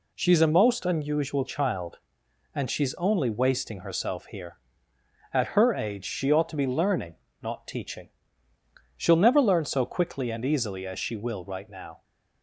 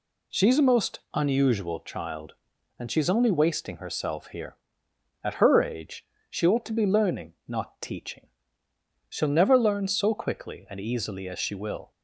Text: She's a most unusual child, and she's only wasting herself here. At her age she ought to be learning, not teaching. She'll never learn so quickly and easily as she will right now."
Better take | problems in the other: first | pauses between "age" and "she"; slight; at 6.0 s; 0.24 s long // stops before "right now"; at 11.9 s

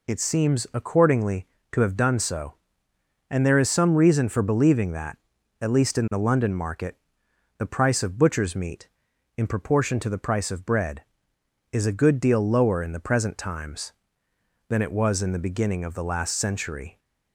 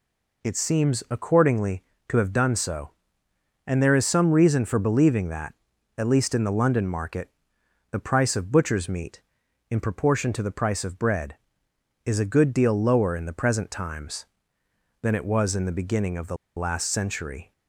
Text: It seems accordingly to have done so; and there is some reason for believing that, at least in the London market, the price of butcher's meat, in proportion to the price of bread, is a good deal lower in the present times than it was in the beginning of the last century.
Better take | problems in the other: first | pauses between "the" and "last"; slight; at 16.3 s; 0.21 s long

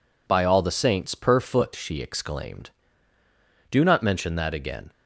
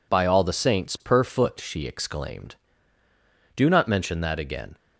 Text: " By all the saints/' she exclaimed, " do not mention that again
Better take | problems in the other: neither | none

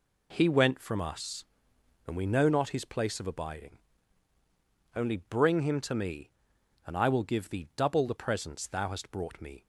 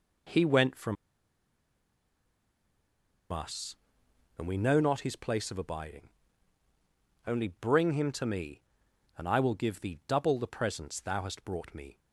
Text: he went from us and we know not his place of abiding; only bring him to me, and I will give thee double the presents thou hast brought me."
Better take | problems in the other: first | pauses between "from" and "us"; strong; at 0.9 s; 2.3 s long

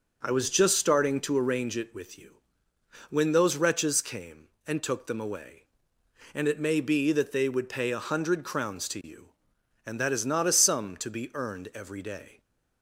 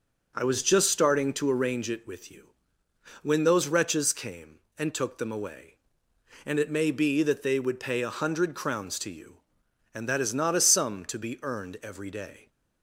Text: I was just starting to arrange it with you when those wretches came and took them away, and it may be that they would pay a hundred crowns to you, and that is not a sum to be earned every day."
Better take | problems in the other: neither | pauses between "you" and "when"; noticeable; the same in both

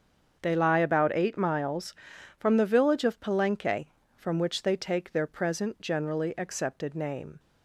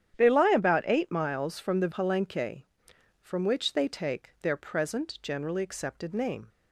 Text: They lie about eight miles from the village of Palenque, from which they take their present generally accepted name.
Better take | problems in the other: first | starts louder than the rest; strong; until 1.2 s; 10 dB; also in the first // skips "village of"; at 1.8 s

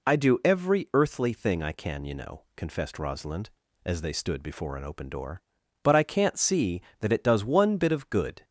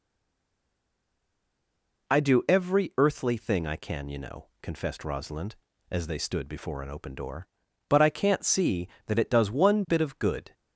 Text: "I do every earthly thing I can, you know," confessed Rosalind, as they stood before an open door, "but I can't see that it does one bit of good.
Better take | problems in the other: first | stays silent before the first word; noticeable; until 2.0 s; 2.0 s long

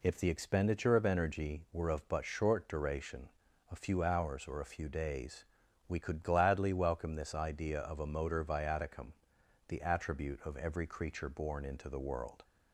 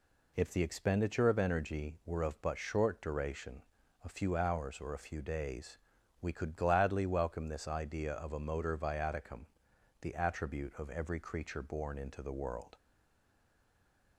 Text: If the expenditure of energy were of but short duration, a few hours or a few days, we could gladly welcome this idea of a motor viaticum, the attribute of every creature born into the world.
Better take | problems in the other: first | stays silent after the last word; noticeable; from 12.7 s on; 1.4 s long

